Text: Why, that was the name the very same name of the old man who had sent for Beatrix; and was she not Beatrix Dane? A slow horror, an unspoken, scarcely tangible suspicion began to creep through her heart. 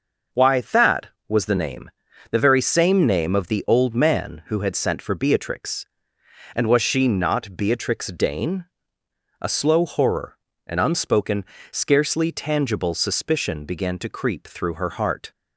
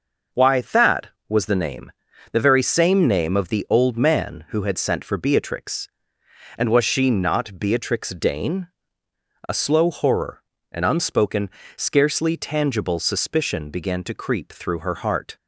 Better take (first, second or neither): neither